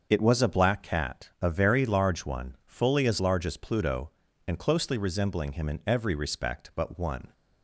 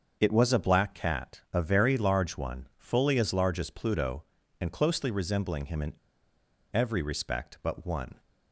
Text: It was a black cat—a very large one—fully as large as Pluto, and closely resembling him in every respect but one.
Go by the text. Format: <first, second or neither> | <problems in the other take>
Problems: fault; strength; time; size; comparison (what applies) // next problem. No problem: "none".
first | starts louder than the rest; until 1.2 s; 6.5 dB; also in the first // pauses between "in" and "every"; noticeable; at 5.9 s; 0.82 s long